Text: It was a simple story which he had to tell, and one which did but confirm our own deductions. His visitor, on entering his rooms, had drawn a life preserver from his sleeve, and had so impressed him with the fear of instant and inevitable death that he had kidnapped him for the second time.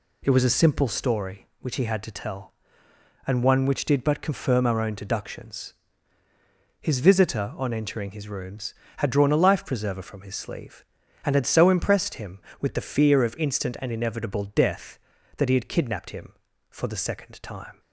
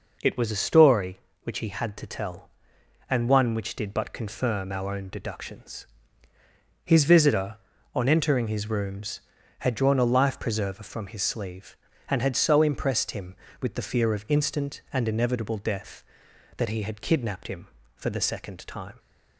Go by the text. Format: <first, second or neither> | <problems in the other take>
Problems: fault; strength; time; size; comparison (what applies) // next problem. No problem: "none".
first | skips "simple"; at 0.6 s